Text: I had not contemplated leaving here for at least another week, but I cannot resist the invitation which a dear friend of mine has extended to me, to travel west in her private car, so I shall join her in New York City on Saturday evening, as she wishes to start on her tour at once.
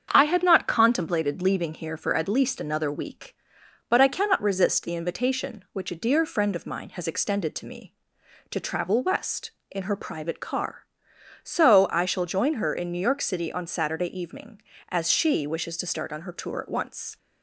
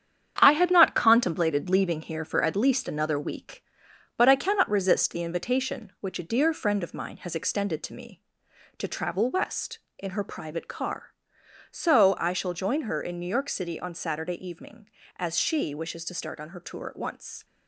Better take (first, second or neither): first